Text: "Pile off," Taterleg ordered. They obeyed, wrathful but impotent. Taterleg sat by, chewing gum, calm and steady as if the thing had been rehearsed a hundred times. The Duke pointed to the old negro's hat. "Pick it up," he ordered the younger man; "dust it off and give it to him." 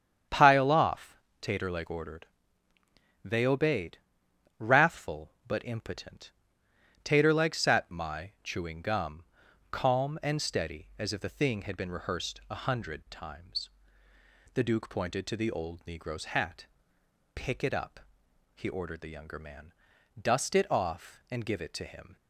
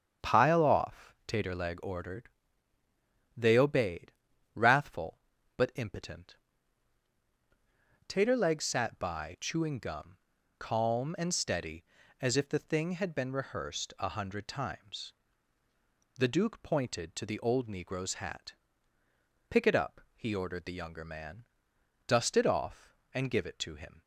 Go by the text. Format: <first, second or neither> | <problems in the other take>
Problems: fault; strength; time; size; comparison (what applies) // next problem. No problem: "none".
second | starts louder than the rest; strong; until 1.5 s; 8.5 dB; strong in the second // says "my" for "by"; at 7.9 s